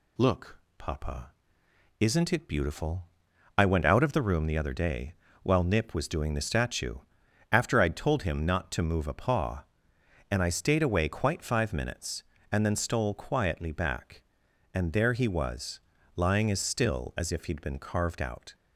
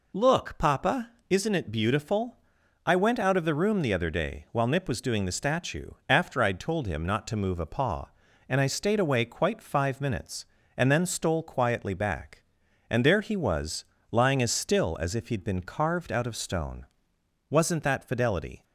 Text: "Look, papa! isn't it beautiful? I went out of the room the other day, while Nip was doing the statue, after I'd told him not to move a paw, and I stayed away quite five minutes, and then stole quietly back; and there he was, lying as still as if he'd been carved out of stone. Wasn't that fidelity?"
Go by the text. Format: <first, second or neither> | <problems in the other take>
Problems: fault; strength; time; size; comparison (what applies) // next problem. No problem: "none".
second | stops before "of stone Wasn't that fidelity"; at 18.5 s